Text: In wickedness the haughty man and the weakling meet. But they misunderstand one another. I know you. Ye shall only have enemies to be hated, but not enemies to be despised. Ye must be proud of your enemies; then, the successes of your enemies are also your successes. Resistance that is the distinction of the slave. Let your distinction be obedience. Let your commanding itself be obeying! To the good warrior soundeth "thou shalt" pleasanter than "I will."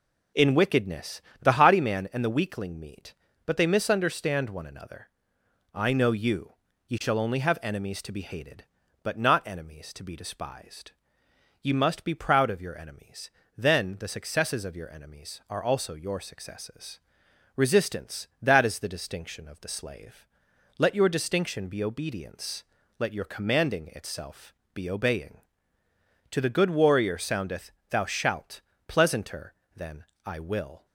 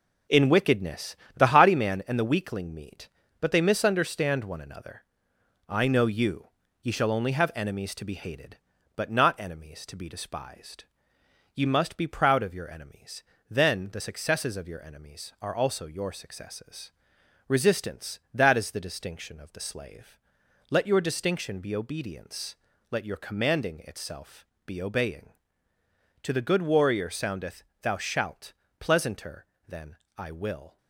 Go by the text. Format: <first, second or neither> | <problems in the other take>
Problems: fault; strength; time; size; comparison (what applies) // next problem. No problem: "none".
first | gets quieter; noticeable; throughout; 6 dB // pauses between "wickedness" and "the"; slight; at 1.1 s; 0.20 s long; slight in the first // pauses between "itself" and "be"; slight; at 24.4 s; 0.20 s long; slight in the first // pauses between "soundeth" and "thou"; slight; at 27.6 s; 0.18 s long; slight in the first // pauses between "shalt" and "pleasanter"; slight; at 28.5 s; 0.26 s long; slight in the first // pauses between "than" and "I"; slight; at 29.9 s; 0.20 s long; slight in the first